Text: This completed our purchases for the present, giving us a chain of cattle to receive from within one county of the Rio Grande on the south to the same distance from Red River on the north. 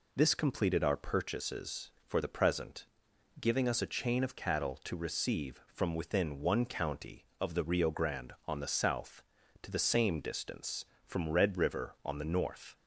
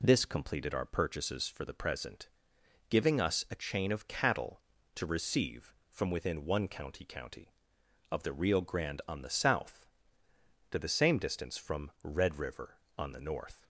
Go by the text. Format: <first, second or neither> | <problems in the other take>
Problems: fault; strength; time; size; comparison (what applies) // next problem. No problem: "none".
first | says "county" twice; at 7.0 s